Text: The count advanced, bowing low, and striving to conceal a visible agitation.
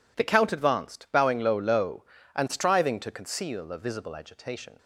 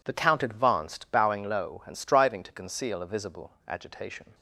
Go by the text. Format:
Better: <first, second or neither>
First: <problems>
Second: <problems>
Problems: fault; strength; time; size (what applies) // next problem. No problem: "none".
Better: second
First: says "low" twice; at 1.5 s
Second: none